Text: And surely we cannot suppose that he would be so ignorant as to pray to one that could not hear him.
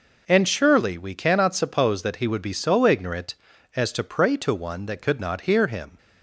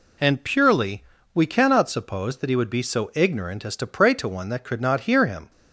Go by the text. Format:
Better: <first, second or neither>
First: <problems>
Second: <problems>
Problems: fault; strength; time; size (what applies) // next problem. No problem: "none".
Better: first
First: none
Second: says "purely" for "surely"; at 0.4 s